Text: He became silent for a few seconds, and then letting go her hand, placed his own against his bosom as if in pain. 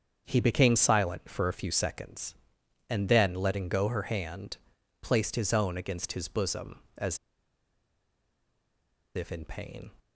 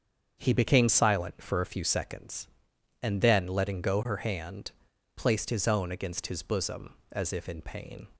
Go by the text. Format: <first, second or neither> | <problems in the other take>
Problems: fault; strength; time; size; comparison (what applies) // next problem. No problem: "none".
second | starts louder than the rest; strong; until 1.2 s; 7 dB; strong in the second // pauses between "as" and "if"; strong; at 7.1 s; 1.9 s long